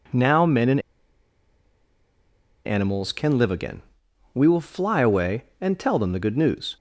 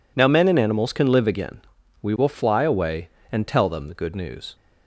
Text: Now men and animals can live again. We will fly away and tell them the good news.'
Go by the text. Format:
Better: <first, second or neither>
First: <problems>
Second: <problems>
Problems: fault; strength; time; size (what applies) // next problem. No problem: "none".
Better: second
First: pauses between "and" and "animals"; strong; at 0.7 s; 1.8 s long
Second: none